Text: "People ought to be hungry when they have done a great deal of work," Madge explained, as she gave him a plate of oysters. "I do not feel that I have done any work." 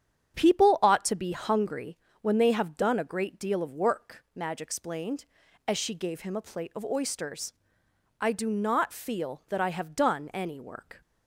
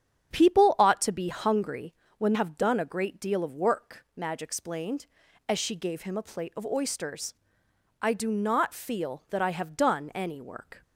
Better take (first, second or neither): first